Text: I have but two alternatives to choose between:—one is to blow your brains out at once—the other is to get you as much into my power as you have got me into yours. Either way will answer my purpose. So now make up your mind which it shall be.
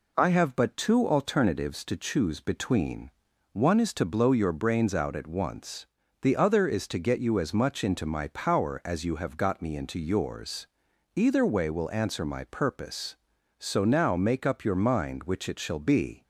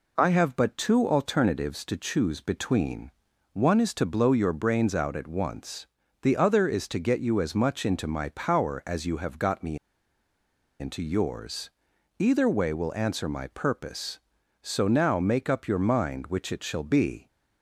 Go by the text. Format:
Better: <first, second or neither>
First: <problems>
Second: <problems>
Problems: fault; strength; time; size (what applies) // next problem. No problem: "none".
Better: first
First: none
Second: pauses between "me" and "into"; at 9.7 s; 1.0 s long